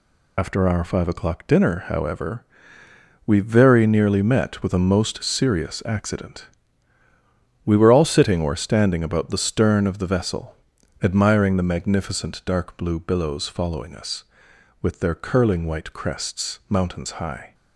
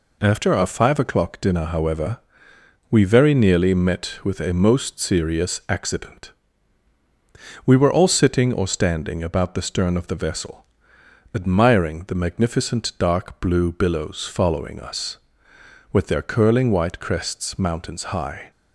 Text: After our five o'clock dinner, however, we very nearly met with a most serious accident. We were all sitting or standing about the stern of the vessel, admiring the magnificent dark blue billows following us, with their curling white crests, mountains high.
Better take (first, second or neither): second